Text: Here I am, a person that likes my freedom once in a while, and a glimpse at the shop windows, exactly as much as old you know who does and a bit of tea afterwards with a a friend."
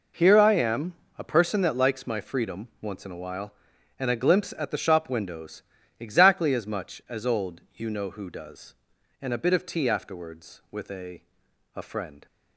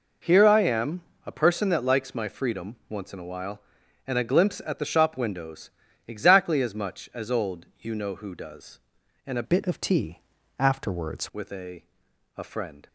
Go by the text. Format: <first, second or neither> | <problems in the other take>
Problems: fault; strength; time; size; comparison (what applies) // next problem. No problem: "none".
first | pauses between "old" and "you"; slight; at 7.6 s; 0.16 s long; slight in the first // changes voice from "bit" to "afterwards"; from 9.4 to 11.2 s; 1.8 s long // pauses between "tea" and "afterwards"; slight; at 10.2 s; 0.36 s long // pauses between "a" and "a"; noticeable; at 11.8 s; 0.54 s long; noticeable in the first